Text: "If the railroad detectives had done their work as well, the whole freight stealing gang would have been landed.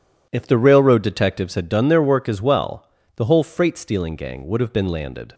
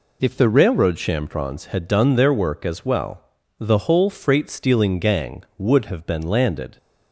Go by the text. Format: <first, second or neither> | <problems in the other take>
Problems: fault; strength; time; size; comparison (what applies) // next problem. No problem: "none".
first | says "chamfrons" for "detectives"; at 0.9 s